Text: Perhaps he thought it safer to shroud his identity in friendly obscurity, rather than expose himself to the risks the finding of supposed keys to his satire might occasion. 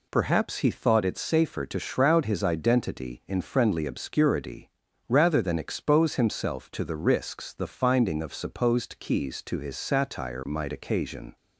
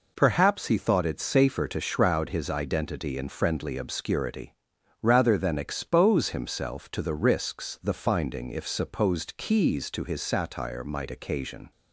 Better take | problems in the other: first | says "if" for "of"; at 8.5 s

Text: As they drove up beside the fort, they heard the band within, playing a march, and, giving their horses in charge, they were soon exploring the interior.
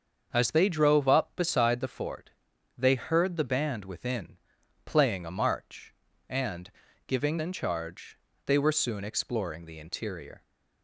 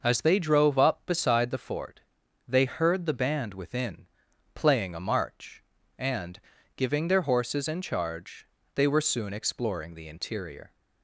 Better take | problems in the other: second | starts louder than the rest; until 1.3 s; 7 dB // skips "their horses"; at 7.3 s

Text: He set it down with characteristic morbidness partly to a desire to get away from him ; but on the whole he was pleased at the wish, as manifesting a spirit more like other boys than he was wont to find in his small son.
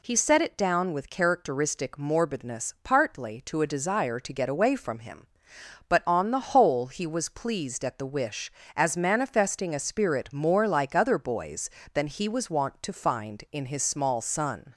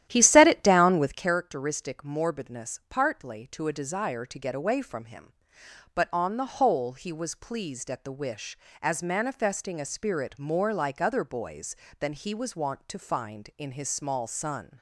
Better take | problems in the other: first | starts louder than the rest; strong; until 1.4 s; 12.5 dB

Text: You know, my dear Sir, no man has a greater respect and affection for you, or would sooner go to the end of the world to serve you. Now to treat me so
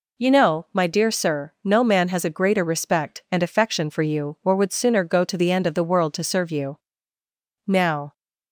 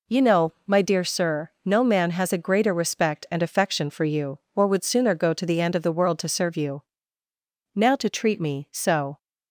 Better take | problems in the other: second | stops before "to treat me so"; at 8.1 s

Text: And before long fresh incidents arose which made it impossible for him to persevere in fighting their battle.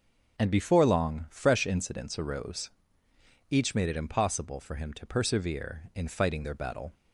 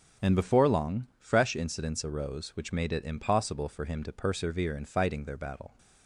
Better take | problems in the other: second | starts louder than the rest; strong; until 1.4 s; 7.5 dB; also in the second // says "each" for "which"; at 3.4 s

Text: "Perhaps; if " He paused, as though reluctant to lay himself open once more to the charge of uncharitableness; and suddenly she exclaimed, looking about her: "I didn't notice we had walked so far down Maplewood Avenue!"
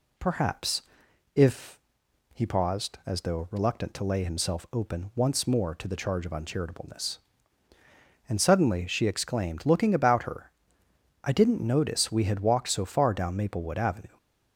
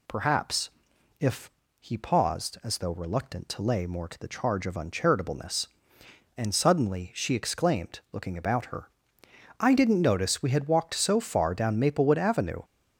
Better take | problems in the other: first | skips "himself open once"; at 3.8 s

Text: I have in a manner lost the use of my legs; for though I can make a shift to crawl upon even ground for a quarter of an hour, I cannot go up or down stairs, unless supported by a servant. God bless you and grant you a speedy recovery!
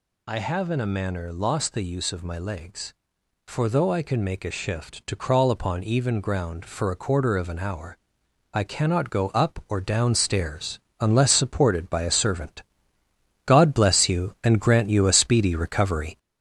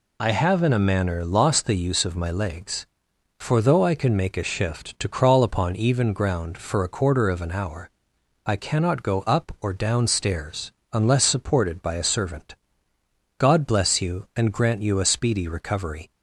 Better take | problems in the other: second | gets louder; noticeable; throughout; 4.5 dB

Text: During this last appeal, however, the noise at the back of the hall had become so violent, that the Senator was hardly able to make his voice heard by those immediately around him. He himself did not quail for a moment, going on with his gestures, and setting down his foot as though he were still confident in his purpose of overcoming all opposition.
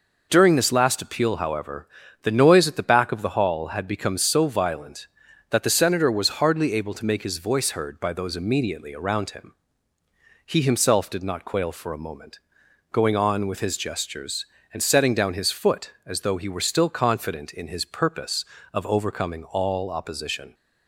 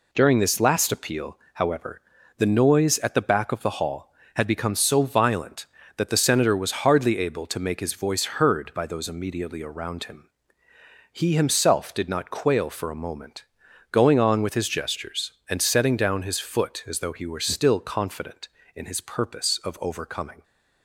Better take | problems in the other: first | stops before "all opposition"; at 20.4 s

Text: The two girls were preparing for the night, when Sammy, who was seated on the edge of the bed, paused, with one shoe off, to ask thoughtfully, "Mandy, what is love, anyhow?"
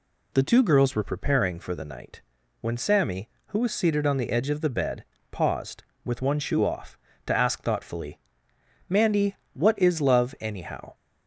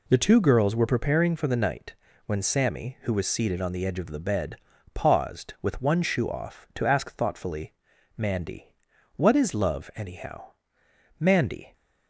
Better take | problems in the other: first | goes on to say "Mandy"; from 11.1 s on; 0.54 s long

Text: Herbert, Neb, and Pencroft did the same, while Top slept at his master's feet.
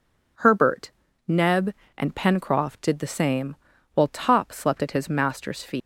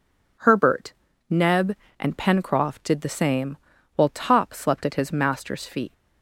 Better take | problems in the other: second | leaves "feet" unfinished; at 5.8 s; 100 ms

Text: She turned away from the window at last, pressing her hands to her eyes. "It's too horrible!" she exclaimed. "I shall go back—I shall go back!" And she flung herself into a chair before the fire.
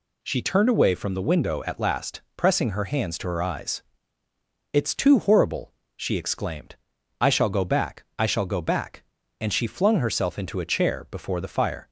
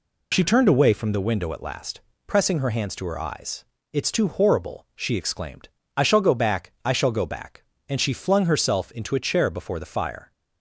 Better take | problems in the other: first | loses the start of "She"; at 0.3 s; 35 ms

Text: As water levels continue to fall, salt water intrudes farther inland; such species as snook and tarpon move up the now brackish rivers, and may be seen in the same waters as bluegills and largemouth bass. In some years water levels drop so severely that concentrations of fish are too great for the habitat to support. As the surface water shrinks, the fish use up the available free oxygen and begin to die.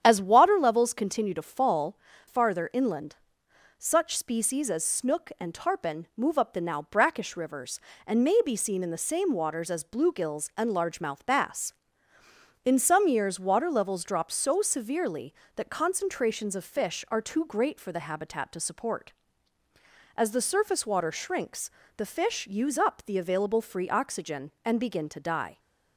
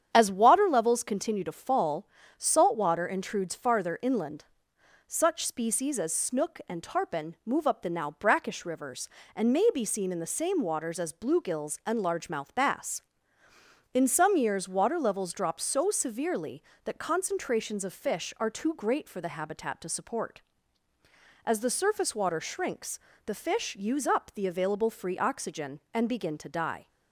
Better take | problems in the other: second | starts louder than the rest; strong; until 1.0 s; 9 dB; strong in the second // skips "salt water intrudes"; at 2.1 s

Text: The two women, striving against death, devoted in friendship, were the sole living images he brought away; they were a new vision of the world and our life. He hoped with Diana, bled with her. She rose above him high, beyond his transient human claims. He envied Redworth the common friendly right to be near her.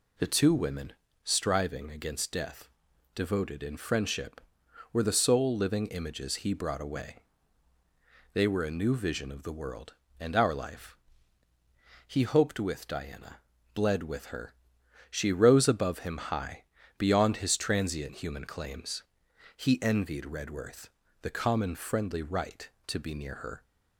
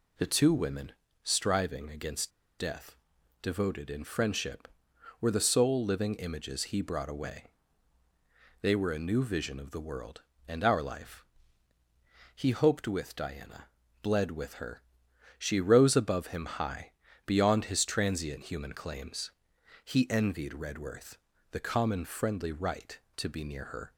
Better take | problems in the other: first | pauses between "against" and "death"; slight; at 2.3 s; 0.28 s long // pauses between "Redworth" and "the"; slight; at 21.1 s; 0.36 s long; slight in the first

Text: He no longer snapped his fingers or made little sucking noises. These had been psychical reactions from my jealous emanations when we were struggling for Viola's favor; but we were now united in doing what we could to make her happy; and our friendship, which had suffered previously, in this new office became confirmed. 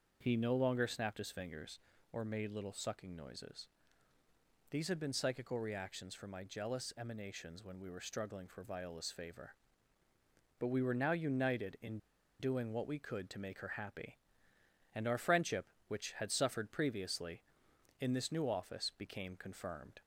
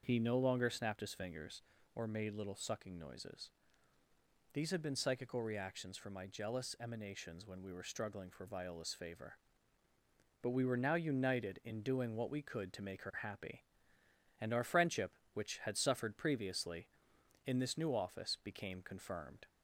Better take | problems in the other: second | starts louder than the rest; until 1.2 s; 6.5 dB; also in the second // pauses between "in" and "doing"; at 11.9 s; 0.41 s long

